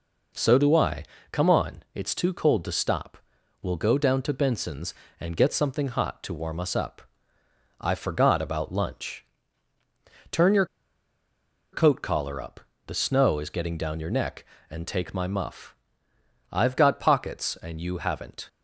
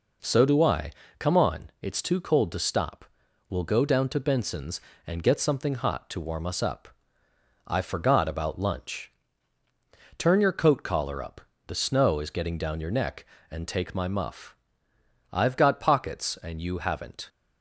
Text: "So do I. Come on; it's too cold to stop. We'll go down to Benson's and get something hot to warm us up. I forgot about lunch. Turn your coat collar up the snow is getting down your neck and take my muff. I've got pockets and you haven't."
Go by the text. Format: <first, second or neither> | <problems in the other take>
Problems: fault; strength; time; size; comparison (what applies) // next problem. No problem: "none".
second | pauses between "your" and "coat"; at 10.6 s; 1.0 s long // pauses between "up" and "the"; slight; at 12.6 s; 0.26 s long; slight in the second